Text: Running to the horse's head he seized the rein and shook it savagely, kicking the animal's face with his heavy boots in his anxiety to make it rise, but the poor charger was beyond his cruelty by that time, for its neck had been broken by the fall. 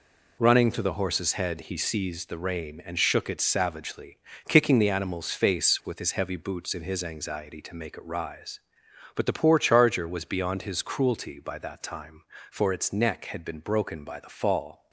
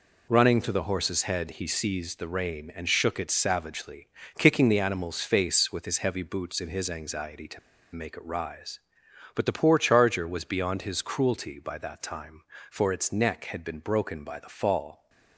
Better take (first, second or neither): first